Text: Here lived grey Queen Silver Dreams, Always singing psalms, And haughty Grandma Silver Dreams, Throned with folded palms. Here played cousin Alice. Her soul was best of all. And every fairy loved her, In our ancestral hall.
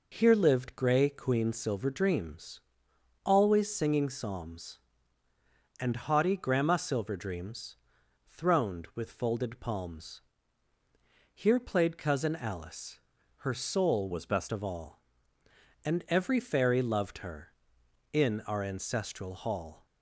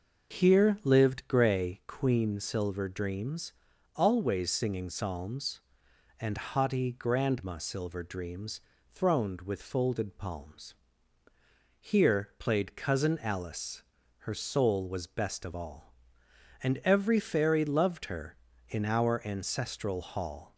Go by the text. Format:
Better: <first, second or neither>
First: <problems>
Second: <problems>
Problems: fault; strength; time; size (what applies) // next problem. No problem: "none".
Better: second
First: changes voice from "was" to "best"; from 14.1 to 14.5 s; 0.4 s long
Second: none